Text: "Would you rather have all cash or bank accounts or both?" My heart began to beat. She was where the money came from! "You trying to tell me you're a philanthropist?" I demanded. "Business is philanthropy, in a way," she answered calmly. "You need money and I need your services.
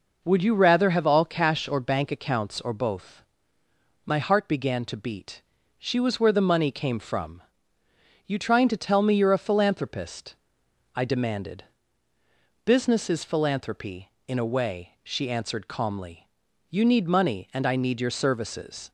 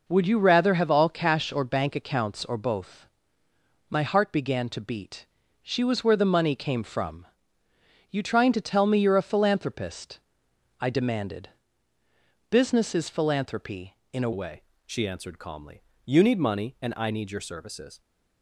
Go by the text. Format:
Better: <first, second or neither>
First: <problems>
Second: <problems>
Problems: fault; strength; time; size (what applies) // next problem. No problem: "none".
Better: first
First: none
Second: changes voice at "way"; from 14.3 s on; 3.7 s long